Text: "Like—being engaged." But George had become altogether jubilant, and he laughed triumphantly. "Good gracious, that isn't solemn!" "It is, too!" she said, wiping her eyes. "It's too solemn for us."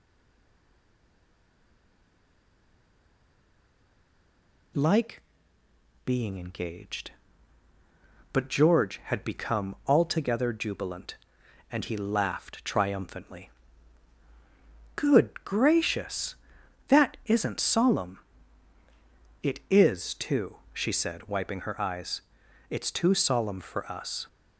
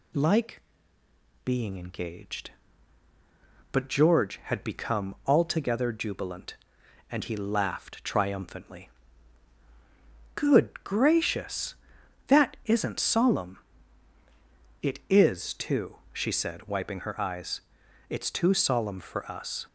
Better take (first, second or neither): second